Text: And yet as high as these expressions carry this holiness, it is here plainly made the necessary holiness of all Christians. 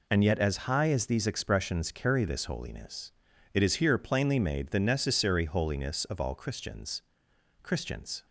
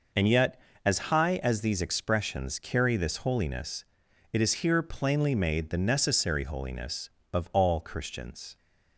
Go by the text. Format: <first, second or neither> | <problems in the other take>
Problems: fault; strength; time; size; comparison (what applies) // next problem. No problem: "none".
second | says "Christians" twice; at 7.6 s